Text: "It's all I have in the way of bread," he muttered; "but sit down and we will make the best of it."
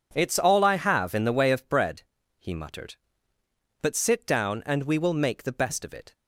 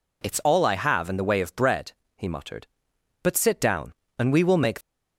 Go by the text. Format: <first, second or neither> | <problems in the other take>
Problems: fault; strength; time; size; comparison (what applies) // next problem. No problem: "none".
first | stops before "the best of it"; at 4.8 s